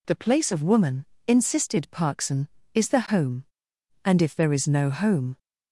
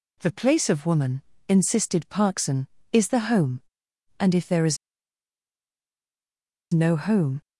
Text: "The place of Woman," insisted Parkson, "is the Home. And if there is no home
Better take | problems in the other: first | pauses between "is" and "no"; strong; at 4.7 s; 1.9 s long

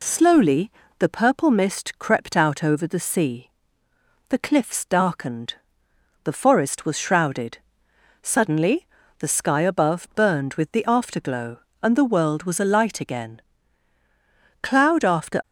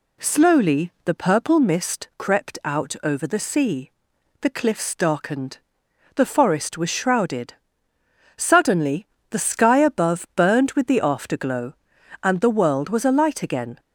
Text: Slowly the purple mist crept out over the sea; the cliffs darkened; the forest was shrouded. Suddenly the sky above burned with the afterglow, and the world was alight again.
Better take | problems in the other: second | pauses between "Slowly" and "the"; slight; at 0.7 s; 0.28 s long // pauses between "Suddenly" and "the"; slight; at 8.8 s; 0.34 s long; slight in the second // goes on to say "Cloud after"; noticeable; from 14.6 s on; 0.80 s long

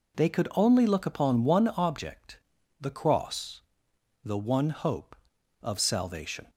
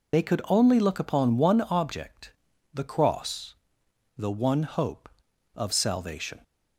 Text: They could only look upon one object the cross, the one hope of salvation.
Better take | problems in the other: first | loses the start of "They"; at 0.1 s; 45 ms // pauses between "object" and "the"; at 2.3 s; 0.40 s long; also in the first

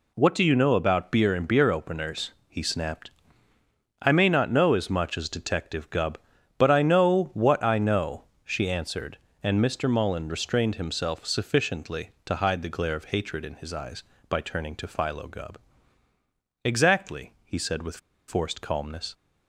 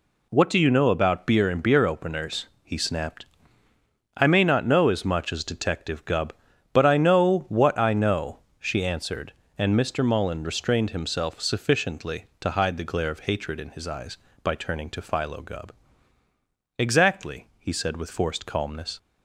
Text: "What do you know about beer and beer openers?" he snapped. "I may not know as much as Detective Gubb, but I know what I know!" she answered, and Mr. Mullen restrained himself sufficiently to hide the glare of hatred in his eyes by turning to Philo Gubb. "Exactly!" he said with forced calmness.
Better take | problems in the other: second | pauses between "with" and "forced"; slight; at 17.9 s; 0.30 s long

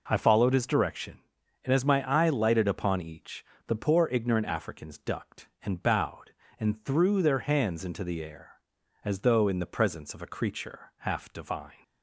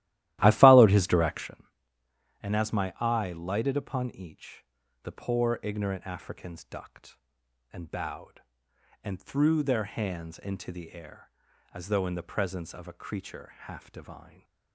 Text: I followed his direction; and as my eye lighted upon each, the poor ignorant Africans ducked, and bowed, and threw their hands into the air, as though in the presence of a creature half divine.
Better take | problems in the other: first | starts louder than the rest; strong; until 1.6 s; 15 dB

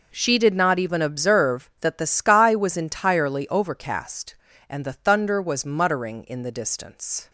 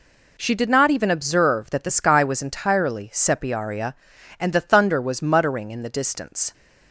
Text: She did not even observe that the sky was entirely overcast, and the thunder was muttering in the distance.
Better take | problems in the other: first | says "sepiaria" for "overcast"; at 3.1 s

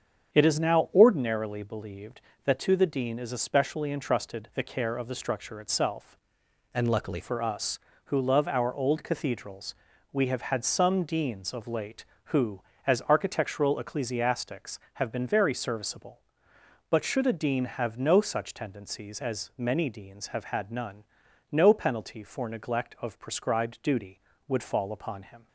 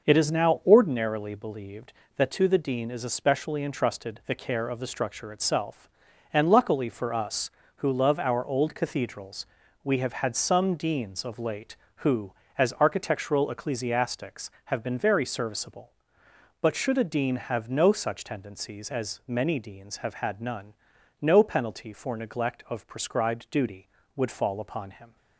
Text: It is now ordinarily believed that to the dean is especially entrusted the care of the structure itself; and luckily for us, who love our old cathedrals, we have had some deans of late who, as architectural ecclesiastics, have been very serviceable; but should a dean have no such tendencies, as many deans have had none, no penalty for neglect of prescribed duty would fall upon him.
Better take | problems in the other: second | starts louder than the rest; strong; until 1.3 s; 8 dB // changes voice from "and" to "luckily"; from 6.7 to 7.1 s; 0.4 s long

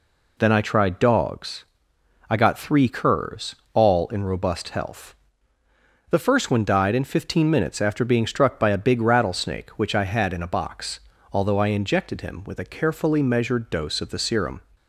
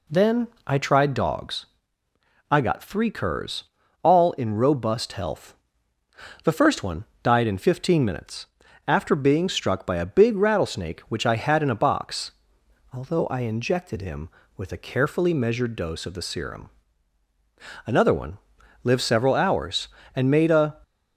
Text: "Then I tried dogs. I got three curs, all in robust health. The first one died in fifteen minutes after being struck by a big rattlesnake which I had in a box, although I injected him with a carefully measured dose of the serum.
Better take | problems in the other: first | pauses between "Then" and "I"; slight; at 0.4 s; 0.18 s long // pauses between "one" and "died"; slight; at 7.0 s; 0.20 s long // pauses between "minutes" and "after"; at 8.4 s; 0.42 s long // goes on to say "Another one lived several hours and made a"; strong; from 17.8 s on; 2.9 s long

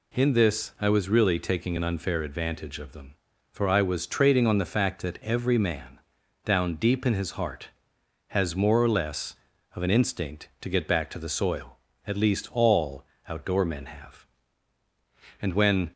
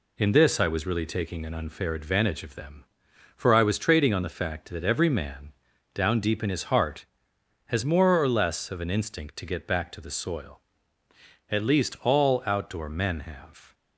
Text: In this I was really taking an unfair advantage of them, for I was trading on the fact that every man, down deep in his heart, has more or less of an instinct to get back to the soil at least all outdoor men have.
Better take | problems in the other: second | pauses between "all" and "outdoor"; slight; at 13.0 s; 0.24 s long // goes on to say "And when"; from 15.3 s on; 0.52 s long

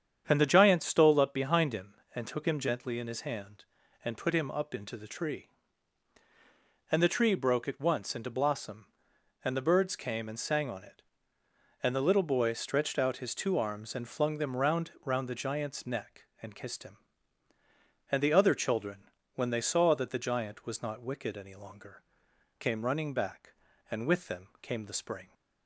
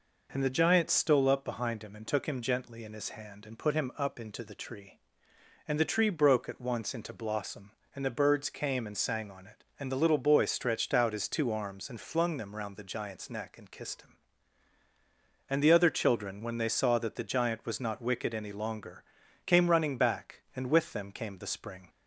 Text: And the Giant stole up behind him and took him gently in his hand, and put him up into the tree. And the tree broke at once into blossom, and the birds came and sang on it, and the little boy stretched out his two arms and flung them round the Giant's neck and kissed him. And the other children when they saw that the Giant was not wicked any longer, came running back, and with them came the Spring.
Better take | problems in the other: second | starts louder than the rest; strong; until 1.3 s; 8 dB // says "round" twice; at 15.0 s // pauses between "children" and "when"; slight; at 19.0 s; 0.26 s long

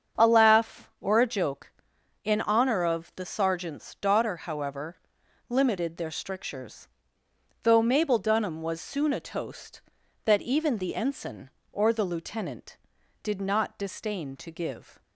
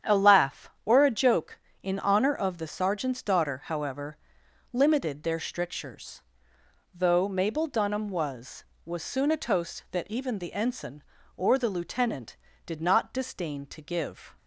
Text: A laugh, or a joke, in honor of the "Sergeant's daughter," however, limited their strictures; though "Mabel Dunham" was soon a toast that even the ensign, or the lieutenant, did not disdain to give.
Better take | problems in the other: first | starts louder than the rest; strong; until 1.2 s; 8.5 dB; strong in the first // says "was" twice; at 8.8 s

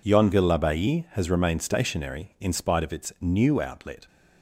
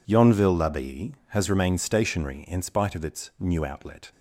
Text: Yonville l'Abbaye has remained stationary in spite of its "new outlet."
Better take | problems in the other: neither | none

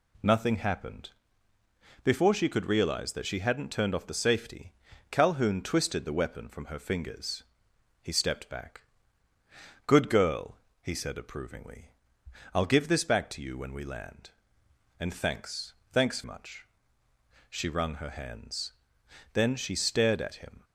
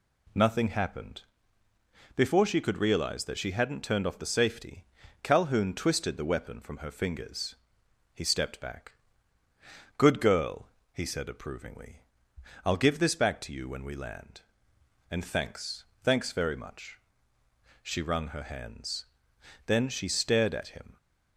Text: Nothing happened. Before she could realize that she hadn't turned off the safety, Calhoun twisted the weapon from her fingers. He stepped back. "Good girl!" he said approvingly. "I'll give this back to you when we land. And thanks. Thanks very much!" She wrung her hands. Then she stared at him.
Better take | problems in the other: second | skips "very"; at 16.2 s

